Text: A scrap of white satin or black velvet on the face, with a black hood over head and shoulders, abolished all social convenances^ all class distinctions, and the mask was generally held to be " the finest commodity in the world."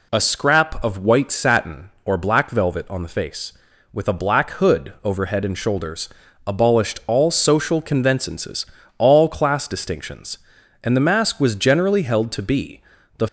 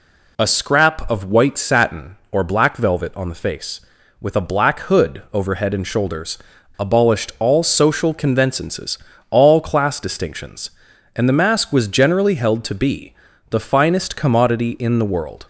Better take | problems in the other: second | pauses between "convenances" and "all"; slight; at 8.6 s; 0.32 s long; slight in the second // stops before "finest commodity in the world"; at 13.2 s

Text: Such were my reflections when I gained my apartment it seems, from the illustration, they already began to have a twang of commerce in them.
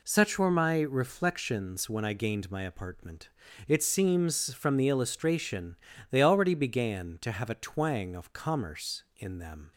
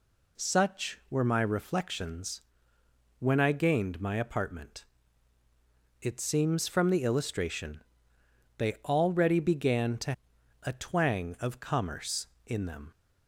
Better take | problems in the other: first | pauses between "reflections" and "when"; noticeable; at 2.4 s; 0.78 s long // pauses between "apartment" and "it"; at 4.8 s; 1.1 s long; also in the first // skips "have"; at 10.3 s

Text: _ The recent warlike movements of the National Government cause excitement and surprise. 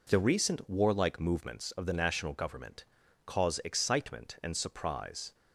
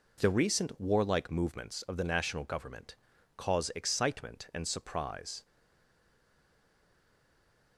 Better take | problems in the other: first | pauses between "Government" and "cause"; at 2.9 s; 0.40 s long; also in the first // stays silent after the last word; from 5.4 s on; 2.3 s long

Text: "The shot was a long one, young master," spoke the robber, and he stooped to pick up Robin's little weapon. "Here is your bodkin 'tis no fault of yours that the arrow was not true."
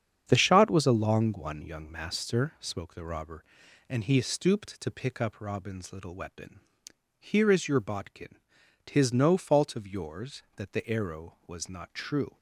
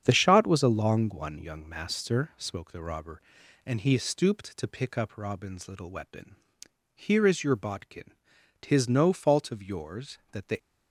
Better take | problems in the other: first | starts louder than the rest; strong; until 1.0 s; 8 dB; strong in the first // pauses between "bodkin" and "tis"; noticeable; at 8.1 s; 0.48 s long; noticeable in the first // stops before "arrow was not true"; at 10.5 s

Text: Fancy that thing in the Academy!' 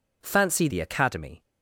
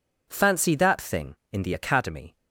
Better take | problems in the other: second | skips "that thing in"; at 0.6 s

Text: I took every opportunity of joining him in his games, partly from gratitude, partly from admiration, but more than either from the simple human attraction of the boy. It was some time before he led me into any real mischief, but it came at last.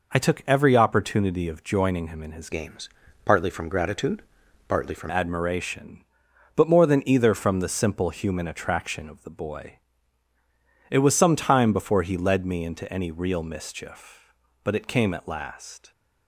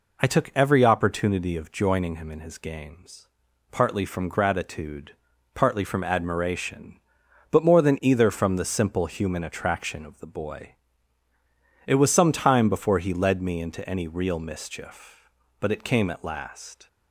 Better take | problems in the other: second | changes voice from "games" to "from"; from 2.4 to 5.0 s; 2.6 s long

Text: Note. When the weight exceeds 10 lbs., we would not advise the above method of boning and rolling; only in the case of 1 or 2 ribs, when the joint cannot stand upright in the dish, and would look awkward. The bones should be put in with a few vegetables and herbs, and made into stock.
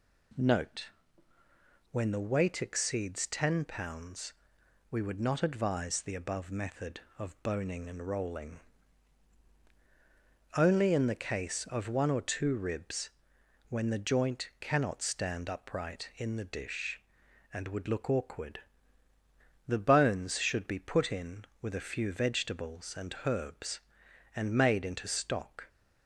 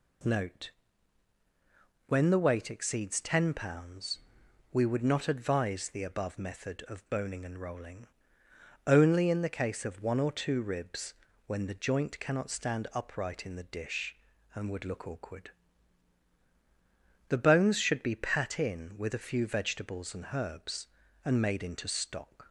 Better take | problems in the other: first | says "pat" for "put"; at 18.1 s

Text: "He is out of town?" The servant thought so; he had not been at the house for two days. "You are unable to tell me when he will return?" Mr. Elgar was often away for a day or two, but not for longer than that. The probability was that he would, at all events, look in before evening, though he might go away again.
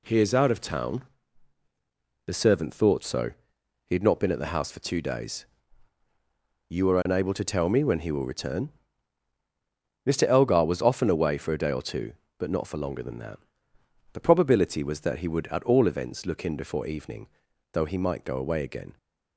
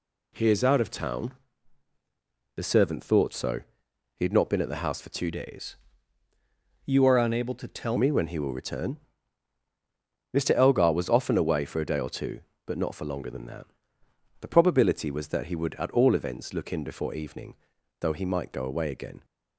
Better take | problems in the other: first | changes voice from "days" to "tell"; from 5.2 to 7.9 s; 2.7 s long

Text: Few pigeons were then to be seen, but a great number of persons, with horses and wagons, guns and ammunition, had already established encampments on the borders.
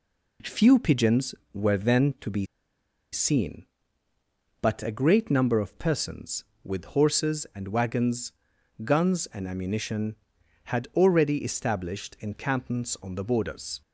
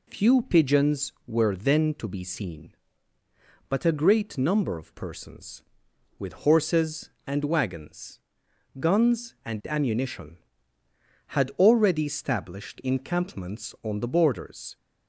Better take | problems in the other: second | pauses between "be" and "seen"; noticeable; at 2.4 s; 0.67 s long

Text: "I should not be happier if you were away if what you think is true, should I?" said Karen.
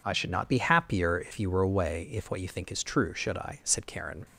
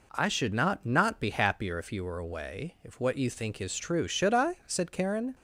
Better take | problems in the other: first | says "not" twice; at 0.8 s

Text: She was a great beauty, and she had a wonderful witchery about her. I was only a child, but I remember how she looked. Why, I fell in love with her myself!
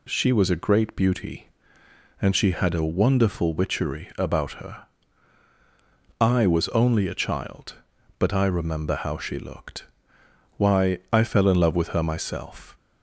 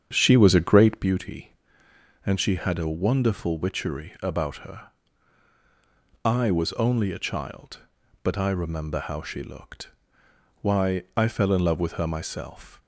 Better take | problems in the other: first | starts louder than the rest; strong; until 1.1 s; 8 dB

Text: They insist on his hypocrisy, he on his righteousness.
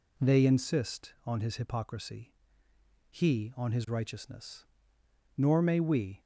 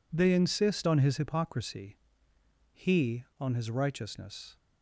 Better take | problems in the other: second | goes on to say "Nor may we"; noticeable; from 5.3 s on; 0.82 s long

